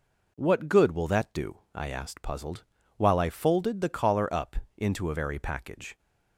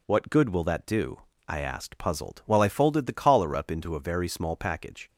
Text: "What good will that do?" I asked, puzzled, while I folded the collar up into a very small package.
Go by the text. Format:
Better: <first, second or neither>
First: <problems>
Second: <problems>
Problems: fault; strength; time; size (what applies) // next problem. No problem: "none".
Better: second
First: pauses between "up" and "into"; slight; at 4.5 s; 0.22 s long // skips "small"; at 5.4 s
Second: none